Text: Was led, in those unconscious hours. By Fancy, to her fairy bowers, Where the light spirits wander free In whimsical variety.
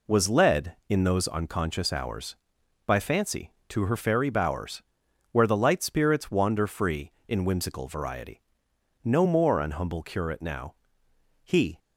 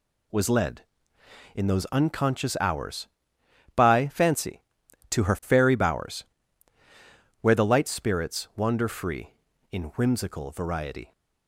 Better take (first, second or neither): second